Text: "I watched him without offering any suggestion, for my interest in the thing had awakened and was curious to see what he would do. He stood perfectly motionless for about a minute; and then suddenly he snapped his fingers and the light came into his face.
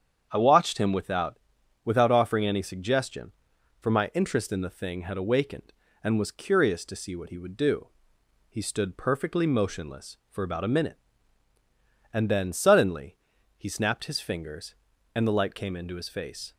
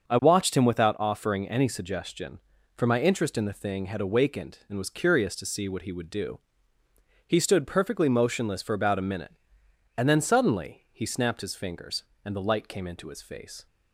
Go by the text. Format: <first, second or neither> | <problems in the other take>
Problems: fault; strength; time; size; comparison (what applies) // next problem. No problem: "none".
second | starts louder than the rest; strong; until 1.3 s; 8 dB; also in the second // says "without" twice; at 1.8 s // pauses between "suddenly" and "he"; at 13.1 s; 0.40 s long